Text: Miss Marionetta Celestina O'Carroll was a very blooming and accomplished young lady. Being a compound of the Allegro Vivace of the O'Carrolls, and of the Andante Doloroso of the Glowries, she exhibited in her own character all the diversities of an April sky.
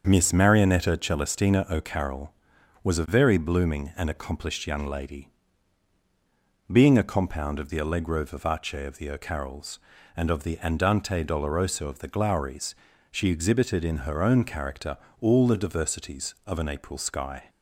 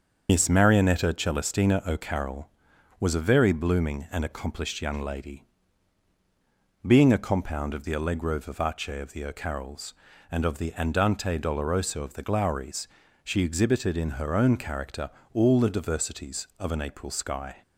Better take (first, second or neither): first